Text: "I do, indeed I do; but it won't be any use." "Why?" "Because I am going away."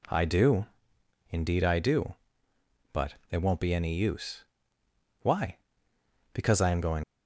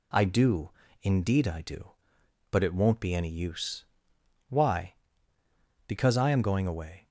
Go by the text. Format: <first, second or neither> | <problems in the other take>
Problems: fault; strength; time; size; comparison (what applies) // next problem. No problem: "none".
second | pauses between "but" and "it"; slight; at 3.1 s; 0.16 s long // stops before "away"; at 7.0 s